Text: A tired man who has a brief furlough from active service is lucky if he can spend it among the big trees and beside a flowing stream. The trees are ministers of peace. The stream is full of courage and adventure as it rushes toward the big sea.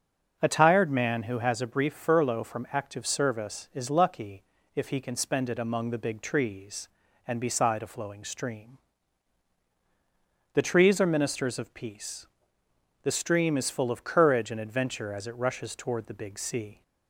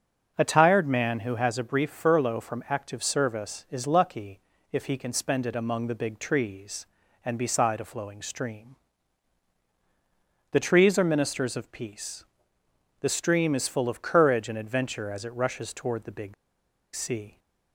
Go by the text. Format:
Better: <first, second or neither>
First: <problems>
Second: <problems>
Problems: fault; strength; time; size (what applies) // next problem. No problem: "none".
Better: first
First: starts louder than the rest; until 1.4 s; 6.5 dB // pauses between "lucky" and "if"; slight; at 4.4 s; 0.32 s long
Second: starts louder than the rest; until 1.3 s; 6.5 dB // pauses between "lucky" and "if"; slight; at 4.3 s; 0.32 s long // pauses between "big" and "sea"; noticeable; at 16.3 s; 0.60 s long